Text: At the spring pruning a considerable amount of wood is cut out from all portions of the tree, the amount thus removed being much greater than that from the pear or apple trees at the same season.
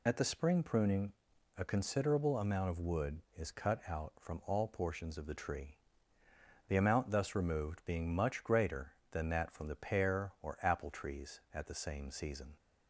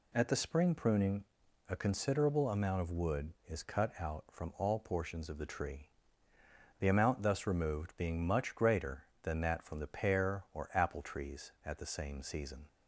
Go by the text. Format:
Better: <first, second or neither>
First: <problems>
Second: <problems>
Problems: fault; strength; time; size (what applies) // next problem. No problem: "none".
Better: second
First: loses the start of "At"; at 0.0 s; 40 ms // pauses between "pruning" and "a"; at 1.1 s; 0.44 s long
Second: pauses between "pruning" and "a"; at 1.2 s; 0.44 s long